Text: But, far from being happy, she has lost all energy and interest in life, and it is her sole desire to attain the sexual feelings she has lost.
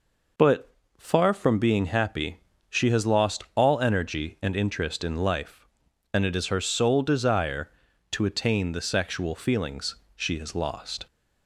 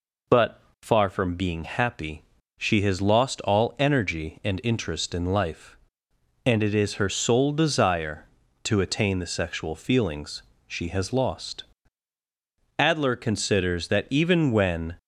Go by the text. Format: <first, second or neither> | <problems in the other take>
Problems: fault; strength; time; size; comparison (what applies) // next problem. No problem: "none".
first | pauses between "feelings" and "she"; slight; at 10.4 s; 0.24 s long; slight in the first // goes on to say "Adler considers that even when"; strong; from 12.7 s on; 2.1 s long